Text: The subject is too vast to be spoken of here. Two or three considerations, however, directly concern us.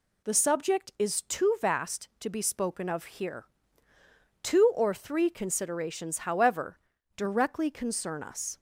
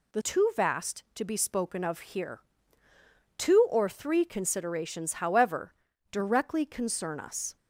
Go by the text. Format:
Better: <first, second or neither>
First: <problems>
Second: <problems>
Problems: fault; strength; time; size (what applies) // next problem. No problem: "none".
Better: first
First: none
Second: skips "subject is"; at 0.2 s